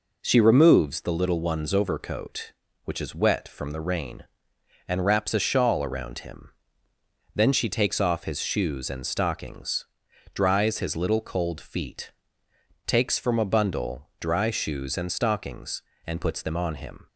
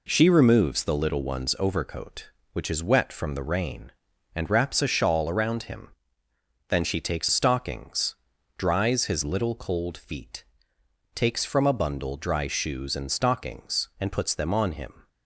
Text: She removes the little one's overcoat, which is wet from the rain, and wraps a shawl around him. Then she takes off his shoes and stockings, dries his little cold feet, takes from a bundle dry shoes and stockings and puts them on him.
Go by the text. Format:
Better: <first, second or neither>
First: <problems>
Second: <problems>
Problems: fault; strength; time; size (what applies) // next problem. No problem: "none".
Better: first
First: none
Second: skips "off his shoes and"; at 7.2 s